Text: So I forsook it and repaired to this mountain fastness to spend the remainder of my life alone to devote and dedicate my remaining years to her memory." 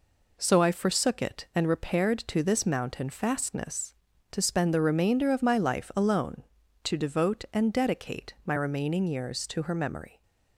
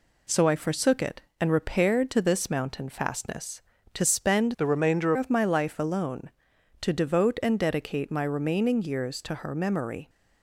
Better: first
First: none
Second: changes voice from "the" to "remainder"; from 4.5 to 5.1 s; 0.6 s long

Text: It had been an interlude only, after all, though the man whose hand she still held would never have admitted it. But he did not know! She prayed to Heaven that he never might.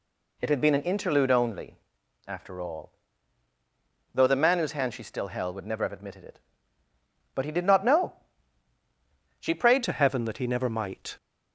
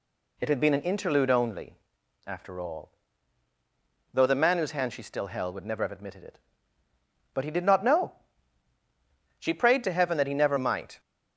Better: second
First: changes voice at "to"; from 9.8 s on; 1.3 s long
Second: none

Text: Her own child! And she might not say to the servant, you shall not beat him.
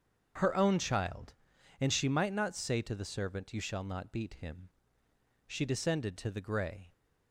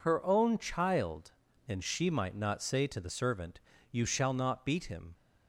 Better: second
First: starts louder than the rest; strong; until 1.8 s; 7.5 dB // goes on to say "She descended to the gray"; from 5.4 s on; 1.4 s long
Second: none

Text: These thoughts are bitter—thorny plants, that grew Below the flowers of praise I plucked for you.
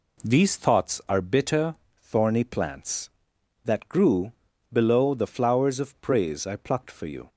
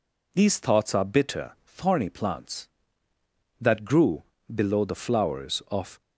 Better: first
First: pauses between "grew" and "Below"; at 4.3 s; 0.38 s long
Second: pauses between "grew" and "Below"; slight; at 4.2 s; 0.30 s long // stops before "praise I plucked for you"; at 6.0 s

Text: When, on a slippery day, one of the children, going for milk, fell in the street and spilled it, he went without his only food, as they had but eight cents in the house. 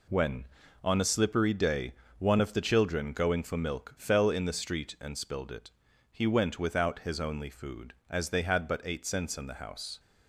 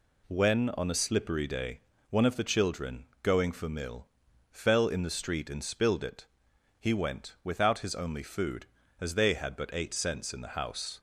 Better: first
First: none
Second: says "mill" for "milk"; at 3.6 s

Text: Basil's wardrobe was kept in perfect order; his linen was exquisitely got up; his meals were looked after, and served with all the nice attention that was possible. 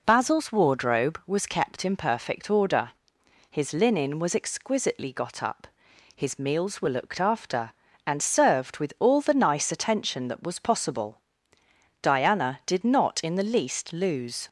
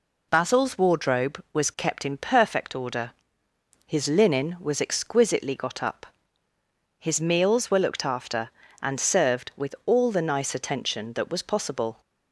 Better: second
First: goes on to say "Diana did not in the least lose"; strong; from 12.0 s on; 2.4 s long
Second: none

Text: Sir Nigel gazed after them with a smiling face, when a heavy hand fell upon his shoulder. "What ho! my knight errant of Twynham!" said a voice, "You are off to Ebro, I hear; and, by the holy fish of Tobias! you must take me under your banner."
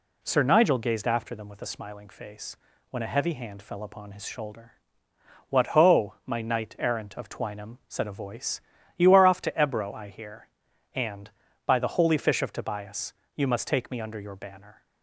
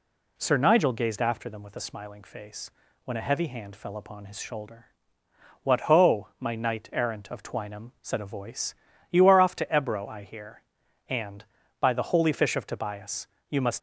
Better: first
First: none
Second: stops before "take me under your banner"; at 13.7 s

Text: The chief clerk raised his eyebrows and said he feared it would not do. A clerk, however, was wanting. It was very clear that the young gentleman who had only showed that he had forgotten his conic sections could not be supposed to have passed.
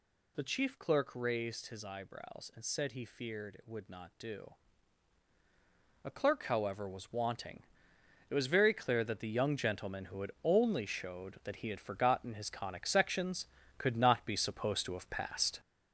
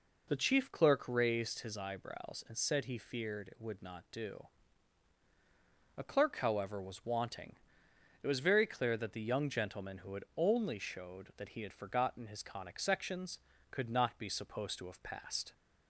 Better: second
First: gets louder; throughout; 6.5 dB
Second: none

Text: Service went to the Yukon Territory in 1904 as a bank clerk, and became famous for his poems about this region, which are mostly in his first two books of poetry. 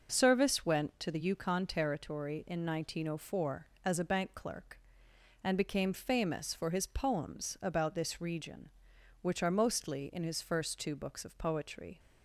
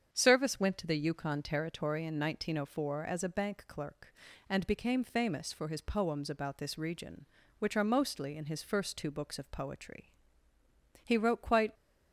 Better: first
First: none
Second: starts louder than the rest; strong; until 1.1 s; 7.5 dB // goes on to say "He wrote quite"; noticeable; from 11.0 s on; 0.68 s long

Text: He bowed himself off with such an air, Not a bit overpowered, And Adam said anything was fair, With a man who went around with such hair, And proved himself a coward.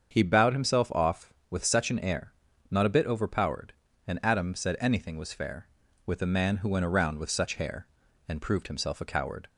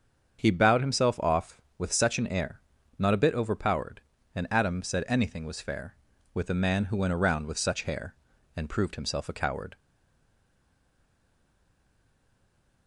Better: first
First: starts louder than the rest; strong; until 1.1 s; 7 dB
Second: starts louder than the rest; strong; until 1.4 s; 7 dB // stays silent after the last word; strong; from 9.7 s on; 3.1 s long

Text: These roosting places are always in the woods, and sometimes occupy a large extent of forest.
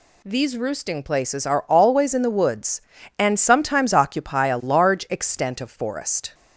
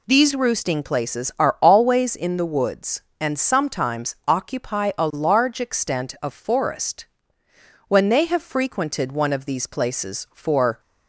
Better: first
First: none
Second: goes on to say "When they have frequented one of these places for"; strong; from 7.8 s on; 2.9 s long

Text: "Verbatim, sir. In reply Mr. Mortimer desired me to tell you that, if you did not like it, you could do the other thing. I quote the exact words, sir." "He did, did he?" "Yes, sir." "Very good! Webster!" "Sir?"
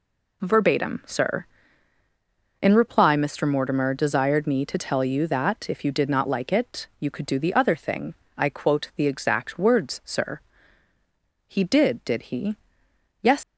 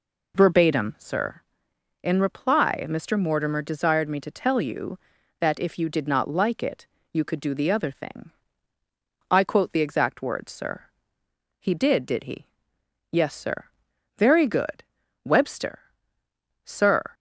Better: second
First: stops before "sir Very good Webster Sir"; at 13.4 s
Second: none

